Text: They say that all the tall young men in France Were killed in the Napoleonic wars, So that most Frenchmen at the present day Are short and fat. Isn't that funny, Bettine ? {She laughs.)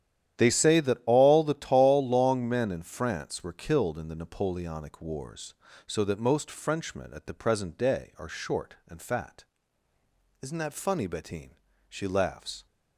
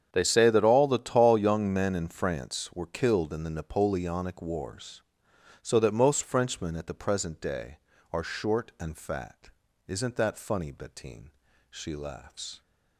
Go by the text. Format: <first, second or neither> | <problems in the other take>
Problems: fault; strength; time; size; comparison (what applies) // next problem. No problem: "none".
second | starts louder than the rest; strong; until 1.4 s; 11 dB; strong in the second // says "long" for "young"; at 2.0 s